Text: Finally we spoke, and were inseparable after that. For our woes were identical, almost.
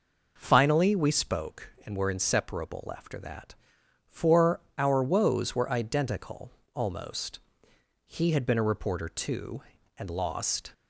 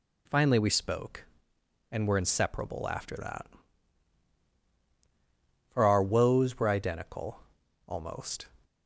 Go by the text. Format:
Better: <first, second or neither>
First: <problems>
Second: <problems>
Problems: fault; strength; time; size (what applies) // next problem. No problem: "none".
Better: second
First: pauses between "For" and "our"; slight; at 4.6 s; 0.16 s long // goes on to say "He had been a reporter too and lost"; strong; from 8.0 s on; 2.6 s long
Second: none